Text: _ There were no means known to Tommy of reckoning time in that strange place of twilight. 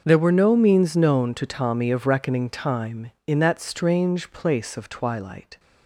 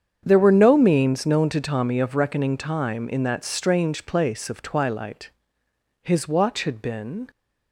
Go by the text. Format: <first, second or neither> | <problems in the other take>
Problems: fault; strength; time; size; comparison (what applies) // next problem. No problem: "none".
first | starts louder than the rest; strong; until 1.2 s; 7.5 dB; also in the first // goes on to say "His watch had been"; noticeable; from 6.0 s on; 1.2 s long